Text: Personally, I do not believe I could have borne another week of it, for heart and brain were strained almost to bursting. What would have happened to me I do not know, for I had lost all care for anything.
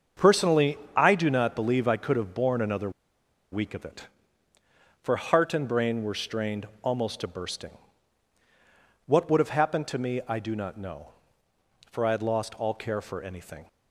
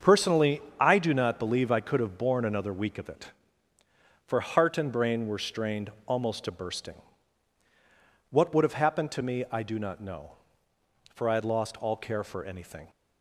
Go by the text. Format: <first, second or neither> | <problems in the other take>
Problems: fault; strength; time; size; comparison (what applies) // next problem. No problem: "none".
second | starts louder than the rest; until 1.3 s; 7 dB; also in the second // pauses between "another" and "week"; noticeable; at 2.8 s; 0.62 s long // pauses between "strained" and "almost"; slight; at 6.6 s; 0.16 s long; slight in the second